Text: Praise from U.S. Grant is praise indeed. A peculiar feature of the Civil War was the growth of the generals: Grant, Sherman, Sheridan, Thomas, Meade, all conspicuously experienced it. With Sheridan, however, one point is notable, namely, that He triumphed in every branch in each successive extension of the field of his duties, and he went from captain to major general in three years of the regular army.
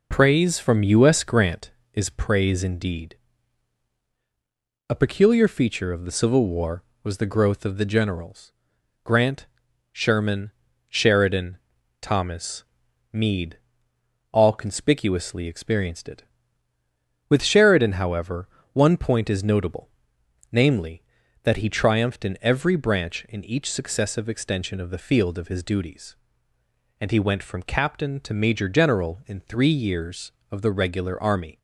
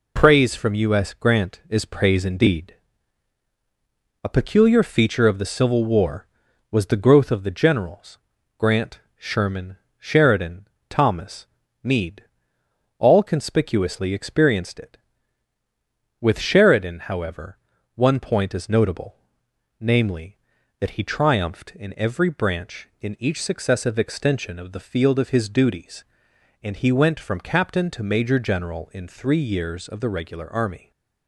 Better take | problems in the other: neither | none

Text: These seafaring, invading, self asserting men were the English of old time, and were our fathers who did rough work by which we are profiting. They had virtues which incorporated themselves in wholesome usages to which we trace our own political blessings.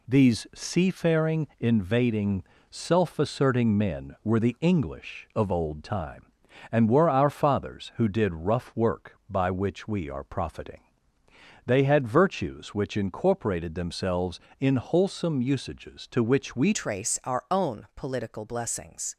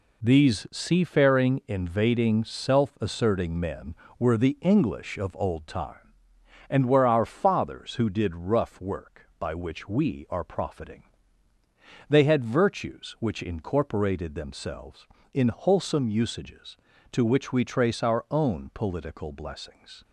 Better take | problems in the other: second | changes voice at "trace"; from 16.7 s on; 2.4 s long

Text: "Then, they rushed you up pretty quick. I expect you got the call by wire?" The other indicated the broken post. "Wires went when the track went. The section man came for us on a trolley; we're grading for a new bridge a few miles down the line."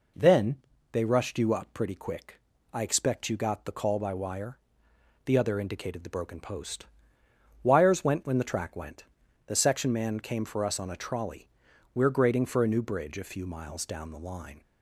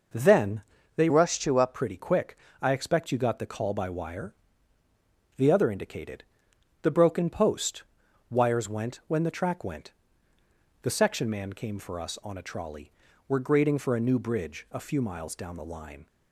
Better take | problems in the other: first | changes voice from "rushed" to "up"; from 1.0 to 1.7 s; 0.7 s long // pauses between "indicated" and "the"; noticeable; at 6.2 s; 0.58 s long

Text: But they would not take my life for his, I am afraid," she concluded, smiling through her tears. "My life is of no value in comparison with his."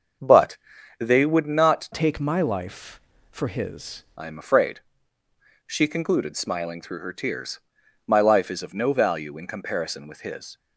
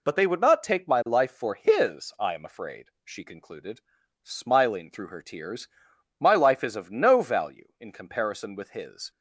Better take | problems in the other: second | starts louder than the rest; until 1.6 s; 6.5 dB // pauses between "But" and "they"; at 0.5 s; 0.42 s long // changes voice from "take" to "his"; from 1.9 to 4.0 s; 2.1 s long

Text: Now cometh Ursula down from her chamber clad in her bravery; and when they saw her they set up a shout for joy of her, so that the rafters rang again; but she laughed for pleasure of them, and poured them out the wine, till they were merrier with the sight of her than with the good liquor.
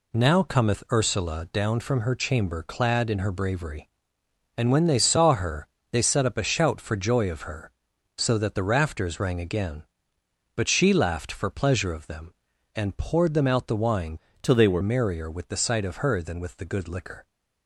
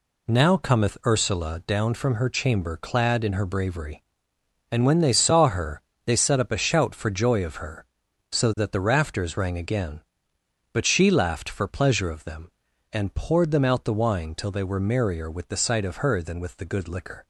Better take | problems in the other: second | pauses between "her" and "they"; slight; at 5.6 s; 0.24 s long; slight in the second // changes voice from "till" to "were"; from 14.4 to 14.8 s; 0.4 s long

